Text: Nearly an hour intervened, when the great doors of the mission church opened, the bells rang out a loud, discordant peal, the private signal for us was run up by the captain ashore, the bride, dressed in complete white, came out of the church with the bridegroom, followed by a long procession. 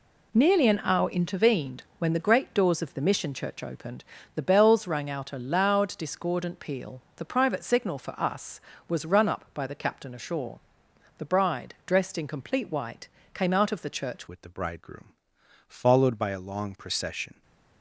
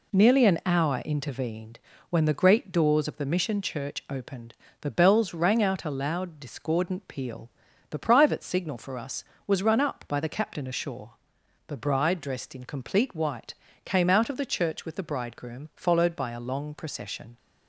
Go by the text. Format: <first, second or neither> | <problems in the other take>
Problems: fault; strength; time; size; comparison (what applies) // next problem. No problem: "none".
second | changes voice at "with"; from 14.2 s on; 3.2 s long